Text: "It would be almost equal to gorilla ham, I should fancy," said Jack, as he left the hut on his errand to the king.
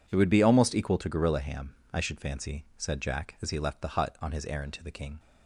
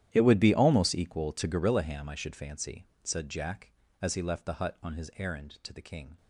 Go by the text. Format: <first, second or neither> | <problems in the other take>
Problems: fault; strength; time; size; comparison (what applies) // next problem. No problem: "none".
first | gets quieter; strong; throughout; 19 dB